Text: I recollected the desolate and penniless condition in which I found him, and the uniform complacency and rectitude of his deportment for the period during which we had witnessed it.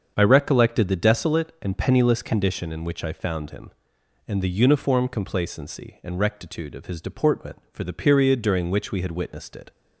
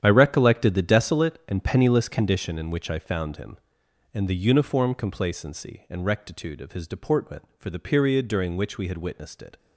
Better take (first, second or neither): first